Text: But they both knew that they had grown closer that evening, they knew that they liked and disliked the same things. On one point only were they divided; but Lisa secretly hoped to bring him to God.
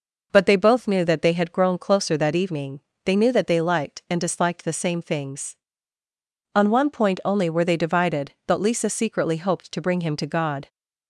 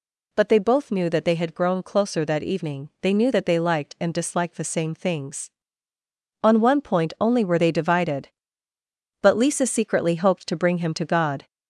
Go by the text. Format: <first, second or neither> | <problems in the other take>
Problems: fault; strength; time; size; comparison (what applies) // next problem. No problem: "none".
first | gets louder; slight; throughout; 3 dB